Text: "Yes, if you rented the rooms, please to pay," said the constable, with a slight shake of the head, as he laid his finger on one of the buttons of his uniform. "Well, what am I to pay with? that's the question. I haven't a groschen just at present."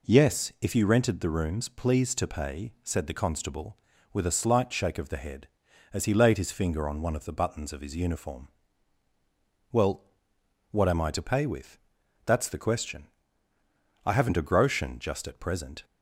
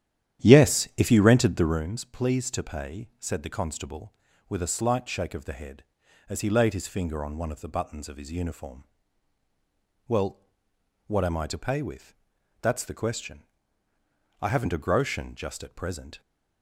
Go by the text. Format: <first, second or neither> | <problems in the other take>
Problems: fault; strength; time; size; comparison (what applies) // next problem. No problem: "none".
first | starts louder than the rest; strong; until 1.8 s; 10.5 dB